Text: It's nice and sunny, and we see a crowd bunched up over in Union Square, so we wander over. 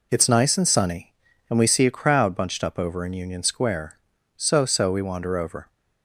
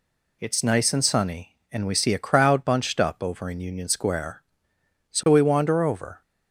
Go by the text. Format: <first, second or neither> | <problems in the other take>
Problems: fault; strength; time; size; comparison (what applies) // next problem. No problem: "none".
second | says "so" twice; at 4.6 s